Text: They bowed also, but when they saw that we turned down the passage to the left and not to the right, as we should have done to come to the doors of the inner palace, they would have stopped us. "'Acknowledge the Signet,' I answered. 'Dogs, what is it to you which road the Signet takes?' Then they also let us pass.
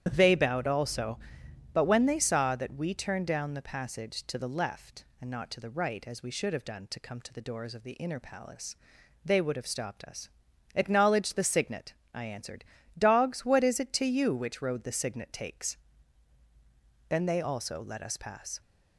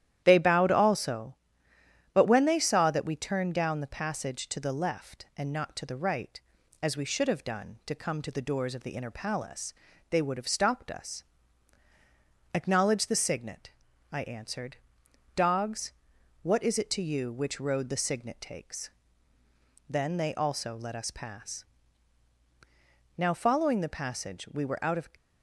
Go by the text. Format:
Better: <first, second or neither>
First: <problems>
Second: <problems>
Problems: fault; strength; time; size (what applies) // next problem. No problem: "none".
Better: first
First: starts louder than the rest; strong; until 1.1 s; 10 dB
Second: starts louder than the rest; strong; until 1.2 s; 11.5 dB // goes on to say "Now following the passage we were out of"; strong; from 23.1 s on; 1.9 s long